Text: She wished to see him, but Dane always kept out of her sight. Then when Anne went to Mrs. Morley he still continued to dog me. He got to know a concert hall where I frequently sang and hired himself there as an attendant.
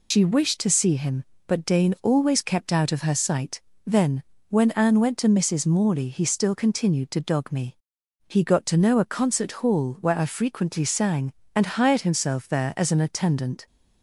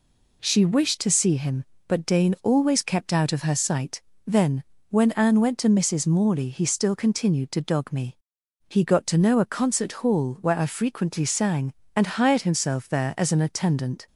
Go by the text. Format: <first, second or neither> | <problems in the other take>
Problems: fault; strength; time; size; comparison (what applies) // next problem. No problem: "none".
second | loses the start of "She"; at 0.1 s; 105 ms // pauses between "Then" and "when"; slight; at 4.2 s; 0.26 s long; slight in the second